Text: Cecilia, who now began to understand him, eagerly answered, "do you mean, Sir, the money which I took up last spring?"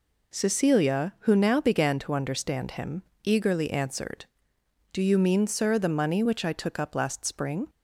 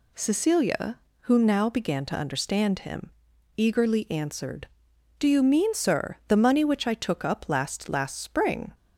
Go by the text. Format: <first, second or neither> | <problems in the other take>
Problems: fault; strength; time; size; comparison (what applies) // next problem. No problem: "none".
first | says "last" twice; at 7.8 s